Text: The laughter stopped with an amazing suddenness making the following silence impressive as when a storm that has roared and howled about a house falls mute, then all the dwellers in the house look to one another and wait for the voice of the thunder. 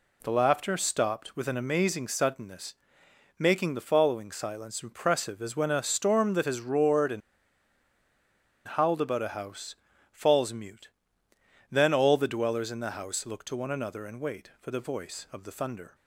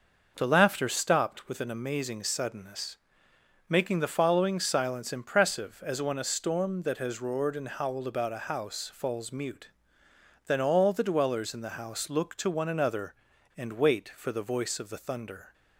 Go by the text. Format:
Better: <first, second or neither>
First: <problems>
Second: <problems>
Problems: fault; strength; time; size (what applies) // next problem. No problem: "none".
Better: second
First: pauses between "suddenness" and "making"; noticeable; at 2.7 s; 0.64 s long // pauses between "and" and "howled"; strong; at 7.2 s; 1.4 s long // pauses between "house" and "falls"; at 9.7 s; 0.38 s long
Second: pauses between "suddenness" and "making"; noticeable; at 2.9 s; 0.70 s long